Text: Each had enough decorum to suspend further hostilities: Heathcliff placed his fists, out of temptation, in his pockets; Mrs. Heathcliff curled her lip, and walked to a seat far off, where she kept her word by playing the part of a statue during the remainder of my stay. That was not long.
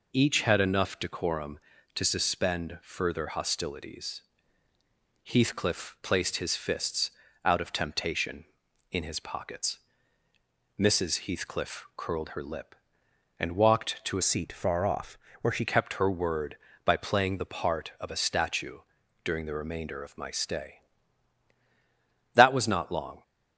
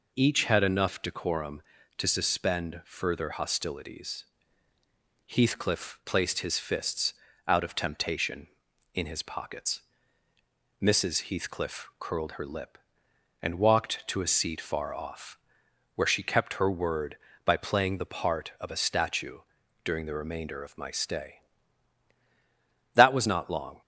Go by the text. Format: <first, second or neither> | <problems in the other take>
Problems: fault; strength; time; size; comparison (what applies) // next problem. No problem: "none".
second | changes voice from "seat" to "she"; from 14.2 to 15.6 s; 1.4 s long // pauses between "statue" and "during"; at 18.7 s; 0.44 s long; also in the second